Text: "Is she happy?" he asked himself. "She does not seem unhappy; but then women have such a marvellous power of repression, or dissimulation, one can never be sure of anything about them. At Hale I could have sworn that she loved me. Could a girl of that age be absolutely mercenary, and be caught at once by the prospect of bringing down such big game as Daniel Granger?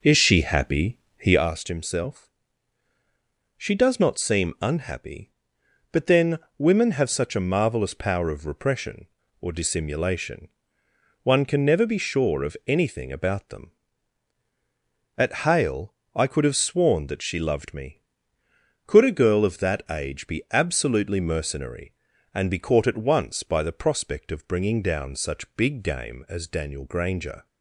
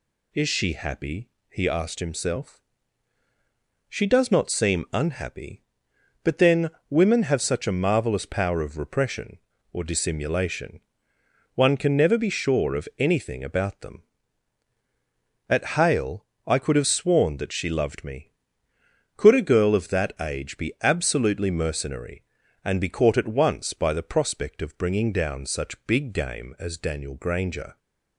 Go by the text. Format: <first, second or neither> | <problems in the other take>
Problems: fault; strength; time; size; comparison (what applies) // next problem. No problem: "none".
second | starts louder than the rest; noticeable; until 1.5 s; 4.5 dB // pauses between "then" and "women"; slight; at 6.3 s; 0.18 s long; slight in the second // pauses between "Hale" and "I"; slight; at 15.9 s; 0.20 s long; slight in the second